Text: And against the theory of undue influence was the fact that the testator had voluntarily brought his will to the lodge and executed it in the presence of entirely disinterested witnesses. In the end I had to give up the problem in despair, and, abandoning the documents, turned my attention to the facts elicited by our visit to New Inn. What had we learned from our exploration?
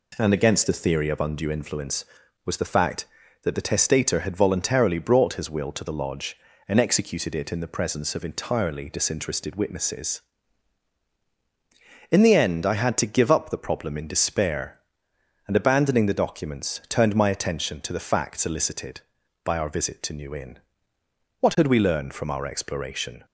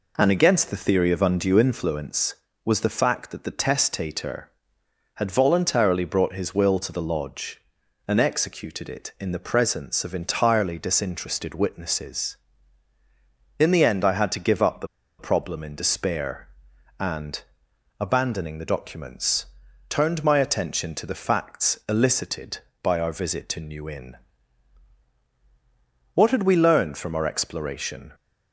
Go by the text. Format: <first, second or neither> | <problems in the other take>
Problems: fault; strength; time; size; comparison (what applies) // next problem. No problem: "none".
first | pauses between "the" and "problem"; slight; at 14.8 s; 0.32 s long